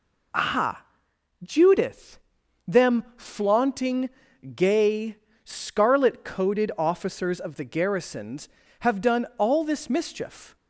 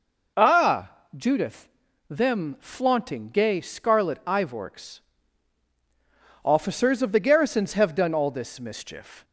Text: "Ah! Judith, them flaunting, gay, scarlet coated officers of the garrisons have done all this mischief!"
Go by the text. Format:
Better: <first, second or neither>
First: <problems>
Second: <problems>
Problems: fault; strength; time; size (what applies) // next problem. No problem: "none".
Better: first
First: none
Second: says "ivorks" for "coated"; at 4.2 s